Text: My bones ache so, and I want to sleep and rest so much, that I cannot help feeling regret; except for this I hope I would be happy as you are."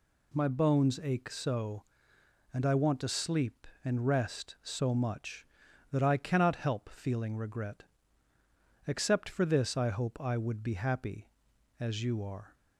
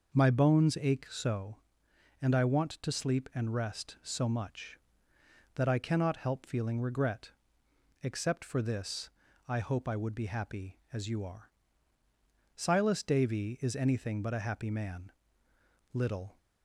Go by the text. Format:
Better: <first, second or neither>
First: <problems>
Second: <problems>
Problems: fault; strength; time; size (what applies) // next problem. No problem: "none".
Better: first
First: none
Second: pauses between "this" and "I"; at 9.0 s; 0.40 s long // goes on to say "Silas Davy is anything but a happy man little"; strong; from 12.5 s on; 3.8 s long